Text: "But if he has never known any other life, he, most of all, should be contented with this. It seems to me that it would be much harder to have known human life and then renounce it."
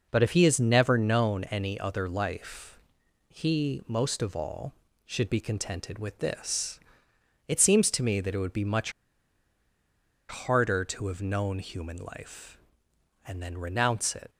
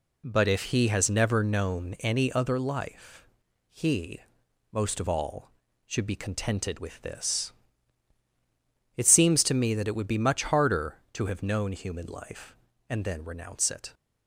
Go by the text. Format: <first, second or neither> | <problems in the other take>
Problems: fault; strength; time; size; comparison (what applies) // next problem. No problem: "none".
second | pauses between "much" and "harder"; strong; at 8.9 s; 1.3 s long